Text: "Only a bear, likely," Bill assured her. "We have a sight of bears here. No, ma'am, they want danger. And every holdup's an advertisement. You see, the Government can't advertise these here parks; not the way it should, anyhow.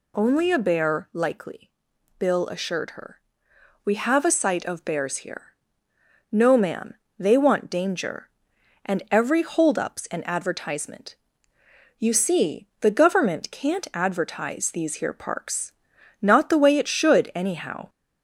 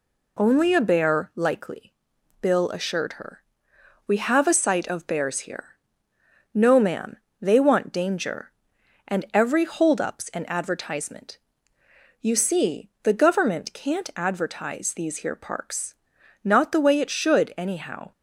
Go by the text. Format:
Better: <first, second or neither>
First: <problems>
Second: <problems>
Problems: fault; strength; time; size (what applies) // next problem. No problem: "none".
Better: second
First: gets louder; slight; throughout; 2.5 dB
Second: none